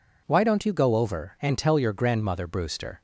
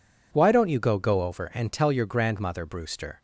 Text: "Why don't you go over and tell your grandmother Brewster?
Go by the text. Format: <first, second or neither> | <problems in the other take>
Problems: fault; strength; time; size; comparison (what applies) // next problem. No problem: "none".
first | says "go" twice; at 0.9 s